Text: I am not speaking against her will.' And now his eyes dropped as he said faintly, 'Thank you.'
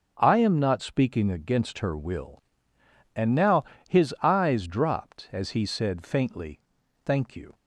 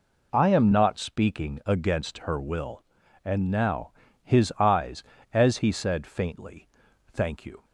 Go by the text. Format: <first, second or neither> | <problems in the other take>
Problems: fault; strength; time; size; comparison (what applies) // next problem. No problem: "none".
first | pauses between "now" and "his"; slight; at 3.9 s; 0.32 s long; slight in the first // skips "dropped"; at 5.1 s